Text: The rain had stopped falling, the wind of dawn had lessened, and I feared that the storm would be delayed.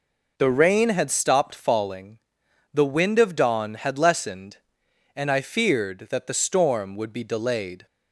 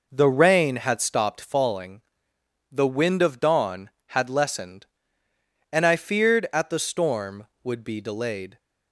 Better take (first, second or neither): first